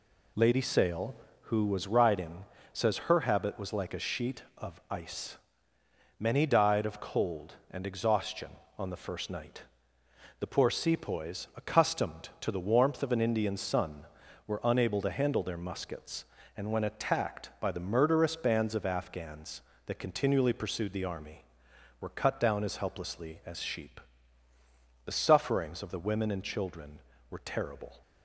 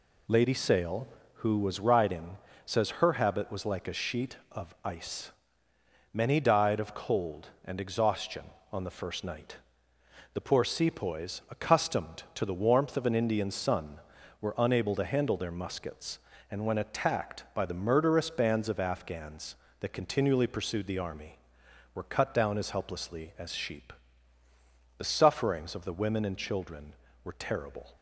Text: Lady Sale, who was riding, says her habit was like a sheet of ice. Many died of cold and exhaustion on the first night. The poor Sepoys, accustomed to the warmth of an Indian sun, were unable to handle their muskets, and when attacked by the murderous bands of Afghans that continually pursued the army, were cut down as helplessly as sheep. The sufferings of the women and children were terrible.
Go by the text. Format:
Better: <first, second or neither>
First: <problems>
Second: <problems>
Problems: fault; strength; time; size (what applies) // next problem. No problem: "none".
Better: neither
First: none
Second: none